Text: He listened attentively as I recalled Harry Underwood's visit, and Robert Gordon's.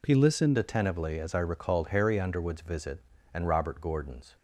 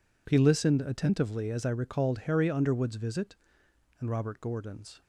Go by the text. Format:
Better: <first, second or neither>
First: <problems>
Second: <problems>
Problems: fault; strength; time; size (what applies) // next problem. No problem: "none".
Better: second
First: changes voice at "attentively"; from 0.5 s on; 3.8 s long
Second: none